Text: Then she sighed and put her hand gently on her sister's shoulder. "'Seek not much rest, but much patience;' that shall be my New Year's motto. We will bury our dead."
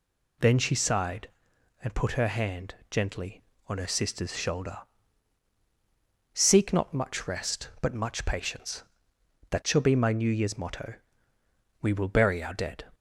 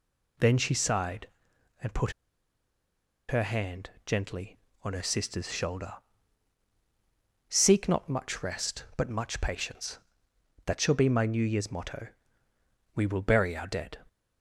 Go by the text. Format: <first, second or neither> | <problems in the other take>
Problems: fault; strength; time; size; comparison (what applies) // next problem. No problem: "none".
first | pauses between "put" and "her"; at 2.1 s; 1.1 s long // pauses between "hand" and "gently"; slight; at 3.8 s; 0.16 s long; slight in the first